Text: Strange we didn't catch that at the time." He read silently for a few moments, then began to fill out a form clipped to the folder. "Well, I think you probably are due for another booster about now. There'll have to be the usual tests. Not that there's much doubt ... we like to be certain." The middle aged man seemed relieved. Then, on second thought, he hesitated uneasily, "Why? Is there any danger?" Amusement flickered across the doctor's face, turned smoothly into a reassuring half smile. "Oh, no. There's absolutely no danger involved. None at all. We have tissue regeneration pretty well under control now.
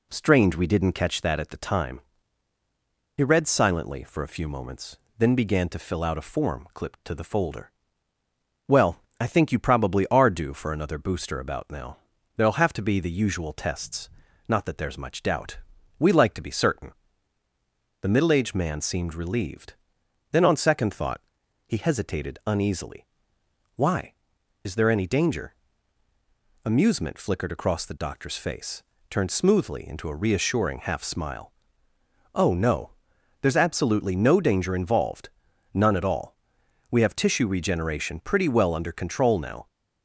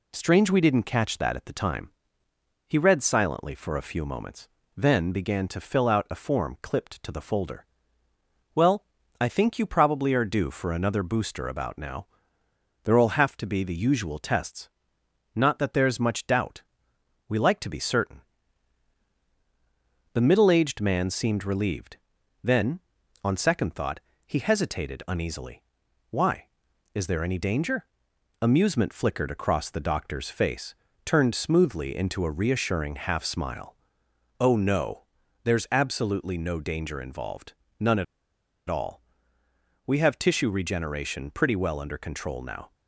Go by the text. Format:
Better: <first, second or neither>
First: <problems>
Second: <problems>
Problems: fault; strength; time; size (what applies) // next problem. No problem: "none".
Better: first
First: none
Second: pauses between "at" and "all"; noticeable; at 38.0 s; 0.64 s long